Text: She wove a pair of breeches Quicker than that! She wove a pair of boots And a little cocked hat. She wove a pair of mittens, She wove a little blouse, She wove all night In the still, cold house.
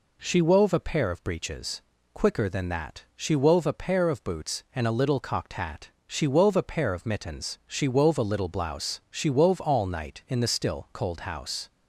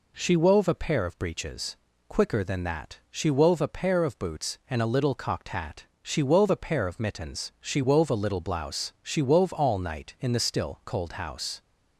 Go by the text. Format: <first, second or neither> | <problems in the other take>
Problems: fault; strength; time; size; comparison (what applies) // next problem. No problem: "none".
neither | pauses between "breeches" and "Quicker"; slight; the same in both